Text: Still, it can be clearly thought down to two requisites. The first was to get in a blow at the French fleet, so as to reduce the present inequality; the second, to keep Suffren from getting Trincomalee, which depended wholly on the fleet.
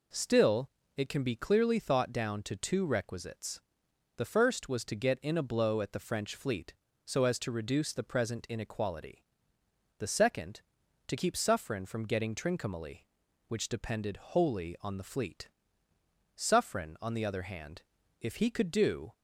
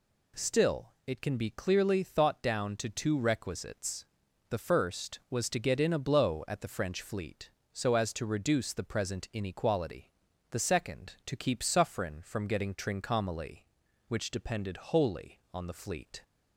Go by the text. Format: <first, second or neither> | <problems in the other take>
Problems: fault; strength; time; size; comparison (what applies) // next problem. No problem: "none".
second | goes on to say "Suffren on the other hand if he could do"; strong; from 16.3 s on; 2.7 s long